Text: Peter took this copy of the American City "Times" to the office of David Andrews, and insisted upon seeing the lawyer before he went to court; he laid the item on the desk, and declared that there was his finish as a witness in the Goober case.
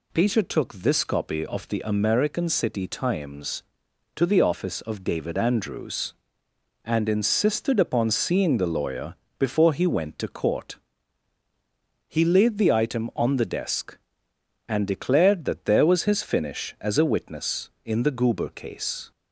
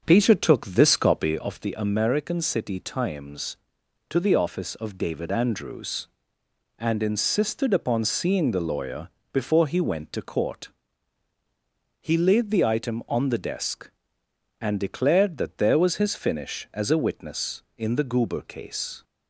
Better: first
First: pauses between "lawyer" and "before"; slight; at 9.1 s; 0.22 s long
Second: starts louder than the rest; until 1.5 s; 6.5 dB // pauses between "lawyer" and "before"; slight; at 9.0 s; 0.22 s long

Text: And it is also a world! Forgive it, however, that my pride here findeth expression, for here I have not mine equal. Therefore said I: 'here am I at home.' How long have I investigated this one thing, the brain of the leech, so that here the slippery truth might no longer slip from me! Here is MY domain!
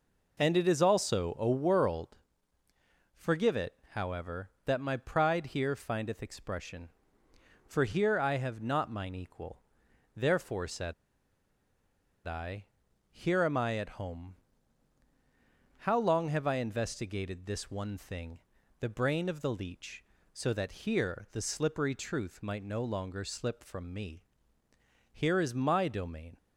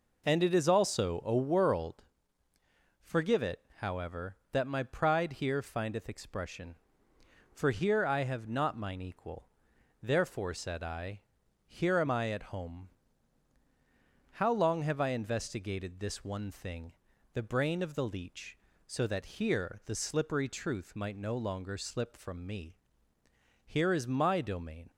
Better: second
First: pauses between "said" and "I"; strong; at 10.9 s; 1.3 s long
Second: none

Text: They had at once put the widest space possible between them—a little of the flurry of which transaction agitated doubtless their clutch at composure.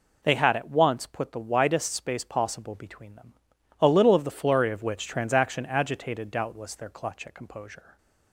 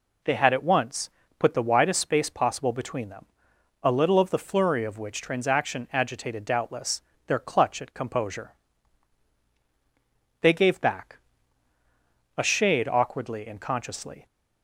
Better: first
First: none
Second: pauses between "once" and "put"; slight; at 1.1 s; 0.28 s long // pauses between "doubtless" and "their"; slight; at 7.0 s; 0.24 s long // goes on to say "They gave back a shade awkwardly and consciously"; strong; from 10.4 s on; 3.8 s long

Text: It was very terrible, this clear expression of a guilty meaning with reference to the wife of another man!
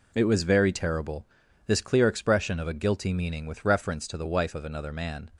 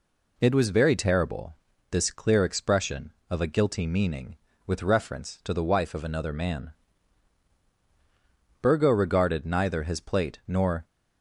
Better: first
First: none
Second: goes on to say "Burgo regarded neither his plate nor"; strong; from 8.5 s on; 2.2 s long

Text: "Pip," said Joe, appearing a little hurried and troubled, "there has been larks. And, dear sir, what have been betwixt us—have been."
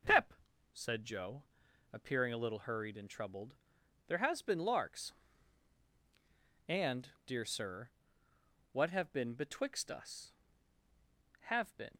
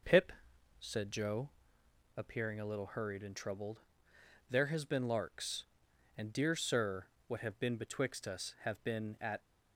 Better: first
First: none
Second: goes on to say "At"; slight; from 9.2 s on; 0.18 s long

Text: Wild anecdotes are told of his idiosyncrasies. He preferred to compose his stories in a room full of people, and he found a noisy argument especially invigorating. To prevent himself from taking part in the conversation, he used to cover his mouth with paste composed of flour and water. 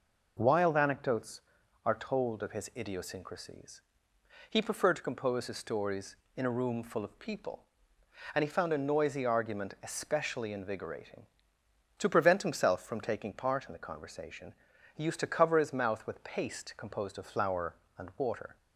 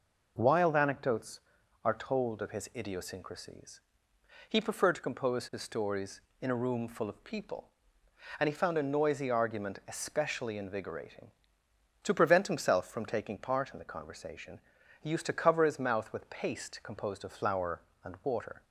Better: neither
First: none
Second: none

